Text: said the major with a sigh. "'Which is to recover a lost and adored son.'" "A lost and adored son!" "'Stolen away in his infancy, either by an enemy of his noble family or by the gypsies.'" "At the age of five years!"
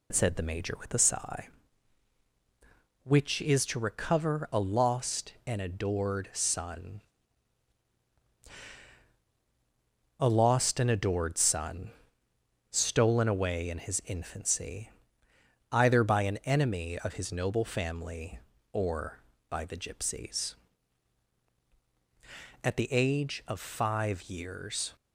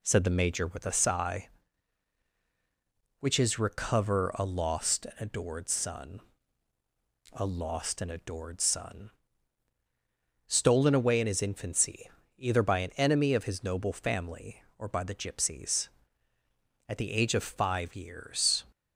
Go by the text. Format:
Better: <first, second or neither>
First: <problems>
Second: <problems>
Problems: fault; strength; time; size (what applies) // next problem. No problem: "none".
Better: first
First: none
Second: skips "to"; at 3.5 s